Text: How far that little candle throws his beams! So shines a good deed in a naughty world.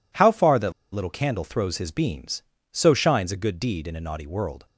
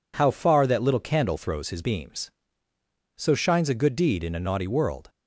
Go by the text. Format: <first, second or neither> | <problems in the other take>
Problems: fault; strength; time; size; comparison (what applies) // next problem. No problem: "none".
second | pauses between "that" and "little"; slight; at 0.7 s; 0.22 s long